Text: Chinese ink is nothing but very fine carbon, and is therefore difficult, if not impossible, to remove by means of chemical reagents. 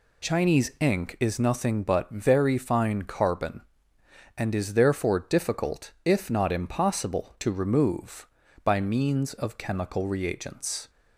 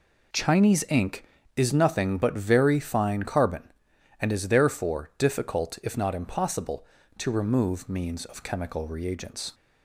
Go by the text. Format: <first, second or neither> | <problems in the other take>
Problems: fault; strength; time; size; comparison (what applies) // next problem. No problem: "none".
first | skips "by"; at 7.8 s